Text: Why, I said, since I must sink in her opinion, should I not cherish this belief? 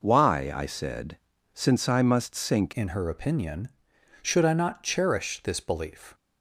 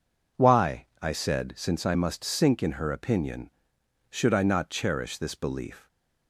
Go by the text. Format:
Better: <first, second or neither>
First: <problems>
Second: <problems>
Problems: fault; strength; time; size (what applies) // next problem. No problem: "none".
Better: second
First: changes voice at "in"; from 2.7 s on; 3.4 s long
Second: none